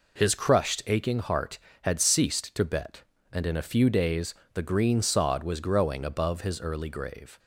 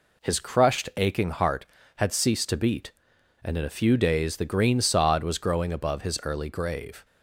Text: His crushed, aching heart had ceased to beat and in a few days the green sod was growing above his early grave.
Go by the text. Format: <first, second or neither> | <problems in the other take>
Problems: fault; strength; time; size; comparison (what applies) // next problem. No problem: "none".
second | says "bet" for "beat"; at 2.6 s // pauses between "days" and "the"; slight; at 4.3 s; 0.22 s long